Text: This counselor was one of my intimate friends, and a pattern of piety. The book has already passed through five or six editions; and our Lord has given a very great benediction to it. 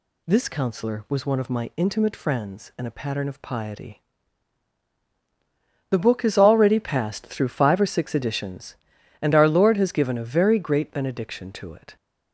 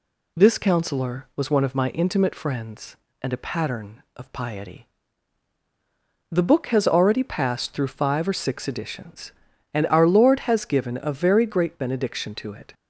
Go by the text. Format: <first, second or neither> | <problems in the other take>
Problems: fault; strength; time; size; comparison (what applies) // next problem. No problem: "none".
neither | none